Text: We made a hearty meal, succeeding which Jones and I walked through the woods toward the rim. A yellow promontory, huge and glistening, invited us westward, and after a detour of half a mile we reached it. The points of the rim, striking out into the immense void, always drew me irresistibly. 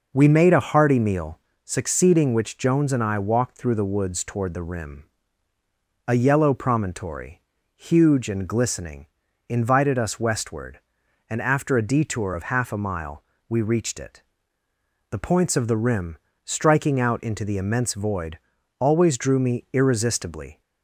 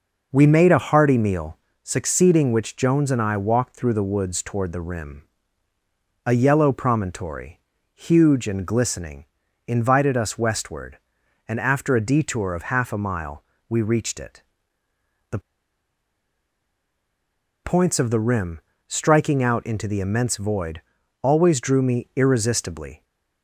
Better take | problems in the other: first | pauses between "mile" and "we"; slight; at 13.4 s; 0.26 s long; slight in the first // pauses between "The" and "points"; strong; at 15.3 s; 2.2 s long

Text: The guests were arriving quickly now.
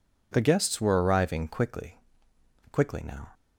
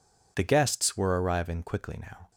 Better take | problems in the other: second | says "quickly" twice; at 2.7 s

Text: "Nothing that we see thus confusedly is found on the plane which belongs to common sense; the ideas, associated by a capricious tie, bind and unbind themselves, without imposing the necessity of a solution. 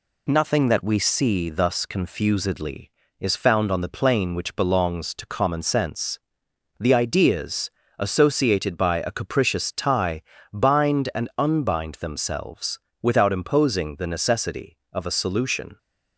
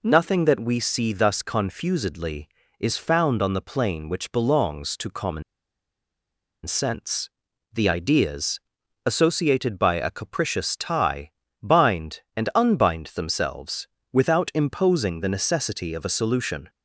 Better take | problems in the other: first | pauses between "common" and "sense"; at 5.4 s; 1.2 s long

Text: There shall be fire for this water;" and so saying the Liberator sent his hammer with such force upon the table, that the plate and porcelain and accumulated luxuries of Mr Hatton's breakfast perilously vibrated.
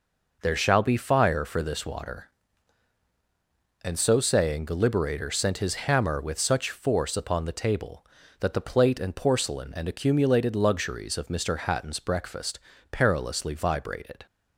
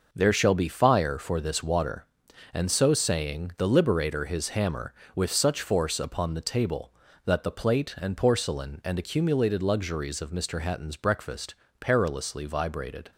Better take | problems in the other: first | skips "sent"; at 4.2 s // pauses between "breakfast" and "perilously"; slight; at 11.5 s; 0.26 s long; slight in the first

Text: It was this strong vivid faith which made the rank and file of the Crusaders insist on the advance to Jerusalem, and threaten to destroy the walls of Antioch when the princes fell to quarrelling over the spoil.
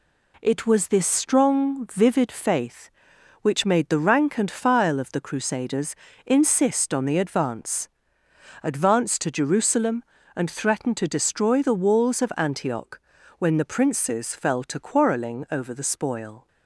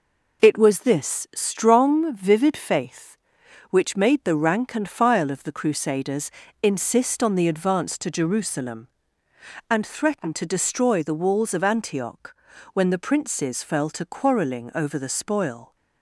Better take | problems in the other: second | pauses between "Crusaders" and "insist"; slight; at 5.9 s; 0.30 s long; slight in the second // says "advance" twice; at 8.6 s // pauses between "Antioch" and "when"; at 12.9 s; 0.40 s long; also in the second

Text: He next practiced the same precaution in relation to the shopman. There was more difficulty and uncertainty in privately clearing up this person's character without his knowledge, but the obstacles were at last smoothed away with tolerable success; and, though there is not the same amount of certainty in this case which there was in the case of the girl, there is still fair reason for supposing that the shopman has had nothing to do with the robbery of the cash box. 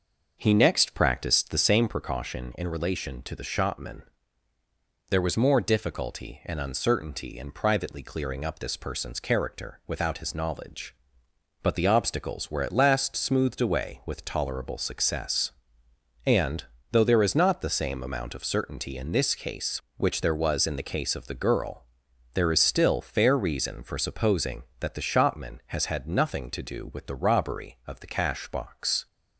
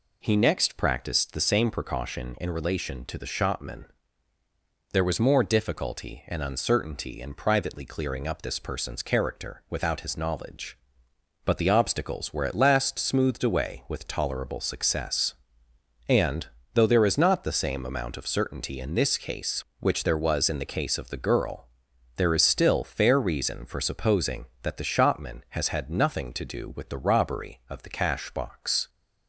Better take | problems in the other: second | starts louder than the rest; noticeable; until 2.0 s; 6 dB

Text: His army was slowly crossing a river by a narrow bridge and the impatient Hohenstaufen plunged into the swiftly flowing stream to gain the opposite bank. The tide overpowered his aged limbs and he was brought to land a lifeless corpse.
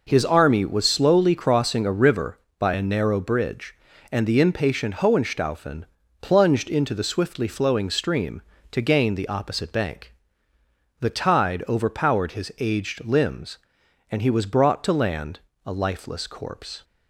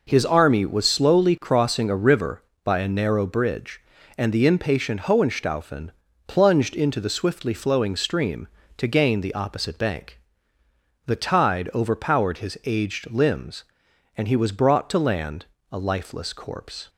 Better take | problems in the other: neither | pauses between "Hohenstaufen" and "plunged"; the same in both // pauses between "land" and "a"; slight; the same in both

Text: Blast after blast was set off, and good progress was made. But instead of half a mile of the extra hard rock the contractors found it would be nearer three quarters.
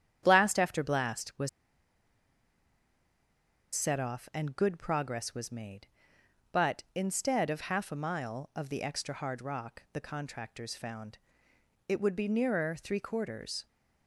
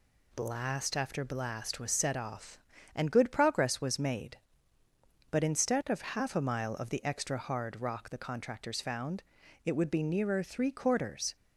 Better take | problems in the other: second | starts louder than the rest; strong; until 1.2 s; 9.5 dB // pauses between "was" and "set"; strong; at 1.4 s; 2.2 s long // pauses between "found" and "it"; noticeable; at 11.1 s; 0.72 s long; also in the second

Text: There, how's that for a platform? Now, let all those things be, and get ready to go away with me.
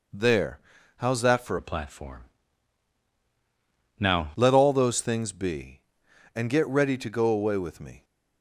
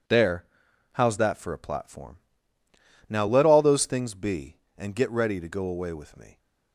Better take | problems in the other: second | changes voice from "a" to "Now"; from 1.5 to 4.2 s; 2.7 s long

